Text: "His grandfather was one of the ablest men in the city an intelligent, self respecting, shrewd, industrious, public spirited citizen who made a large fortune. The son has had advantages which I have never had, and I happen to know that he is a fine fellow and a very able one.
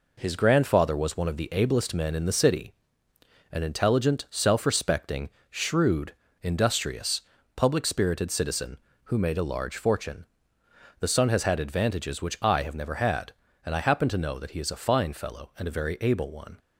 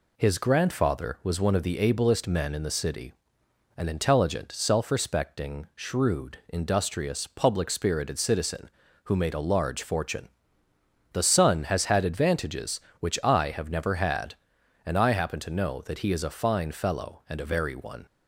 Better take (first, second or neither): first